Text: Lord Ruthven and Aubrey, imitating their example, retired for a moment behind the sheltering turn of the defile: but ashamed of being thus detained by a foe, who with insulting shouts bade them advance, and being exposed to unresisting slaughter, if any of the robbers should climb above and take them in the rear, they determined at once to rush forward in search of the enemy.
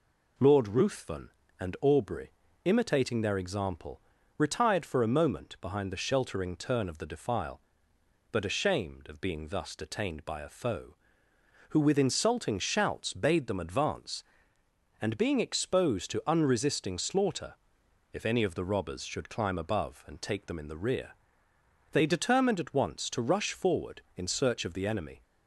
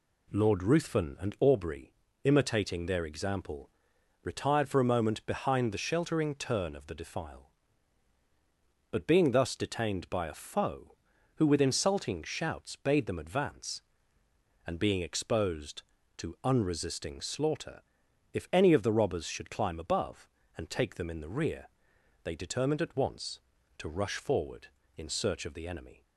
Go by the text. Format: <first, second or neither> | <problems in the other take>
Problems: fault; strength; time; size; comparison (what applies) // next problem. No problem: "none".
first | skips "ashamed of"; at 9.0 s